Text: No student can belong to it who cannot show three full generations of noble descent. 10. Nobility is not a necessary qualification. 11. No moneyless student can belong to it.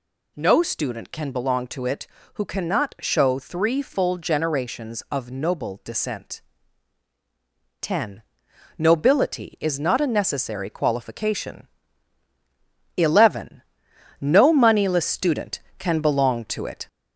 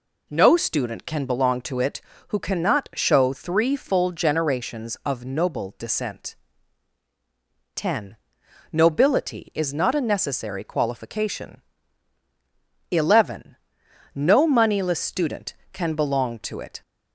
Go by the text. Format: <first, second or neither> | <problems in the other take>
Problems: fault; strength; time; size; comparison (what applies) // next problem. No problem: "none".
second | gets louder; slight; throughout; 2.5 dB